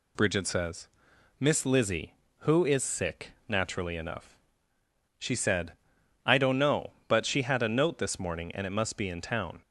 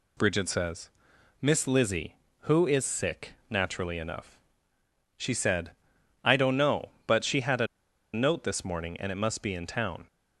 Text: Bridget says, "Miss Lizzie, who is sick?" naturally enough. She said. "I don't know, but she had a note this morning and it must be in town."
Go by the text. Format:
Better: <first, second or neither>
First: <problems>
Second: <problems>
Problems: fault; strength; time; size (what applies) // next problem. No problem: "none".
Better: first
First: none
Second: pauses between "a" and "note"; noticeable; at 7.6 s; 0.47 s long